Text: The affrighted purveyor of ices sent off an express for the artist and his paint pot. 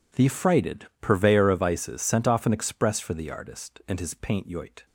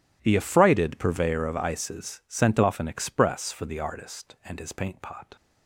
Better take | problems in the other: second | says "yoit" for "pot"; at 4.4 s

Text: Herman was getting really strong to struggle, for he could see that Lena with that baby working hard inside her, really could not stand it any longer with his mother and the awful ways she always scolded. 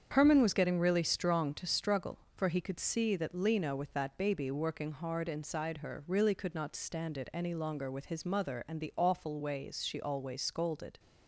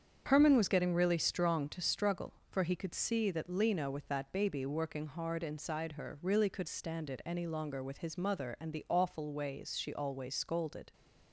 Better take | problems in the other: first | starts louder than the rest; strong; until 1.2 s; 7.5 dB; strong in the first // skips "not"; at 6.6 s

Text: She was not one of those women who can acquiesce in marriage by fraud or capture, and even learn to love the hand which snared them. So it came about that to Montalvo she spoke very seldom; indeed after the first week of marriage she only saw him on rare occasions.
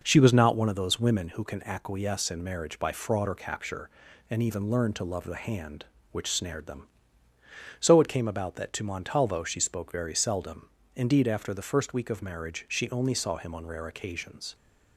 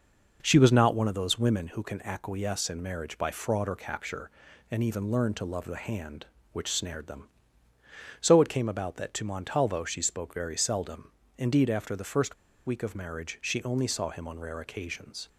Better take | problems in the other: first | pauses between "first" and "week"; slight; at 12.3 s; 0.31 s long

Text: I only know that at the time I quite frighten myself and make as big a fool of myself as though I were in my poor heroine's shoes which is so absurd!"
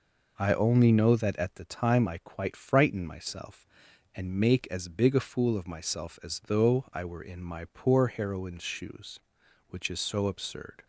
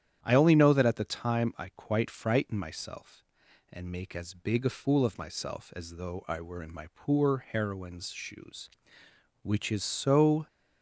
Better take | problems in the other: first | starts louder than the rest; strong; until 1.2 s; 10 dB // stops before "absurd"; at 10.4 s

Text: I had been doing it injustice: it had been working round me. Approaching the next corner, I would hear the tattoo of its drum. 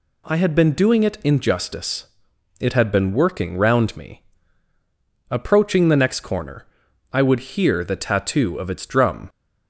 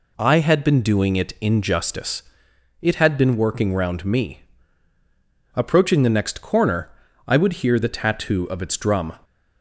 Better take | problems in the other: neither | none

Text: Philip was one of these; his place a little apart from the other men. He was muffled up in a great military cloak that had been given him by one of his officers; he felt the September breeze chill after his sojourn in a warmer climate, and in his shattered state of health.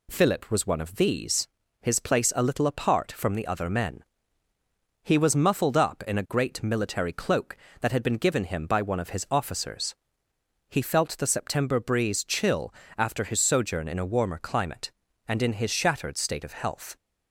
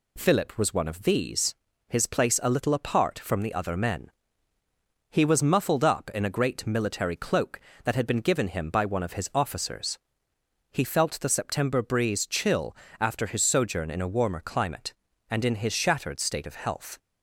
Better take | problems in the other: neither | pauses between "chill" and "after"; slight; the same in both

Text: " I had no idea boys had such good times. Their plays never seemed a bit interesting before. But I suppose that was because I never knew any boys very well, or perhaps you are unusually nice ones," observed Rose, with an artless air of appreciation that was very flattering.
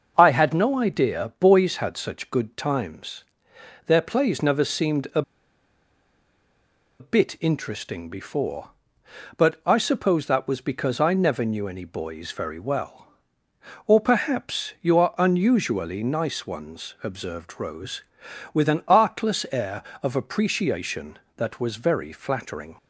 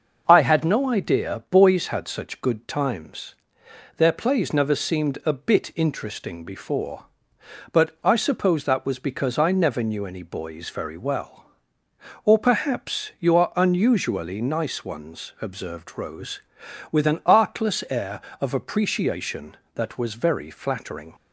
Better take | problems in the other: second | starts louder than the rest; noticeable; until 1.1 s; 6 dB; noticeable in the second // pauses between "a" and "bit"; strong; at 5.2 s; 1.7 s long

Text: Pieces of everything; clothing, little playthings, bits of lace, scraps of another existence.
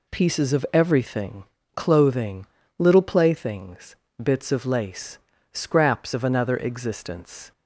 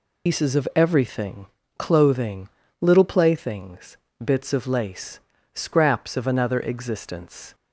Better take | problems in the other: first | loses the start of "Pieces"; at 0.2 s; 140 ms

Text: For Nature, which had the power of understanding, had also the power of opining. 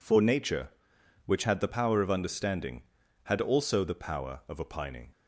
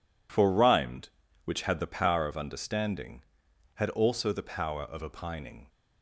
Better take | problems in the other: first | says "Rhymed" for "Nature"; at 0.4 s

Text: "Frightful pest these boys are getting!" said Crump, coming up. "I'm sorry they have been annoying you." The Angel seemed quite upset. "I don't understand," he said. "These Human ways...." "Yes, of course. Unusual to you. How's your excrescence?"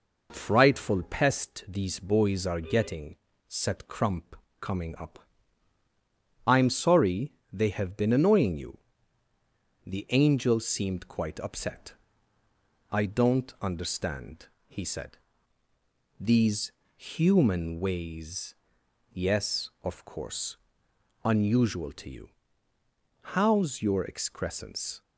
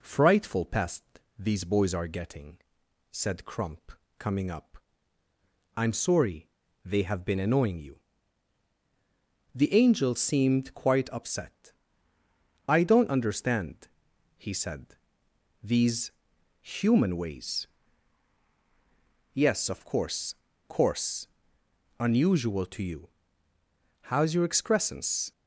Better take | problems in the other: first | pauses between "pest" and "these"; slight; at 1.0 s; 0.34 s long // pauses between "sorry" and "they"; slight; at 6.4 s; 0.34 s long; slight in the first // pauses between "These" and "Human"; noticeable; at 16.0 s; 0.52 s long; slight in the first // says "course" twice; at 20.6 s

